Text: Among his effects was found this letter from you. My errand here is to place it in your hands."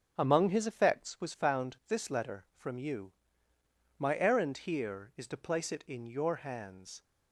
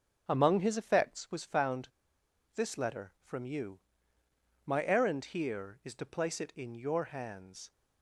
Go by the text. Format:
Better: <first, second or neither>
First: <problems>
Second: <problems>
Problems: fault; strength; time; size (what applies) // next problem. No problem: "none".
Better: first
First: starts louder than the rest; until 1.1 s; 7 dB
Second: starts louder than the rest; until 1.2 s; 6.5 dB // pauses between "found" and "this"; noticeable; at 1.8 s; 0.65 s long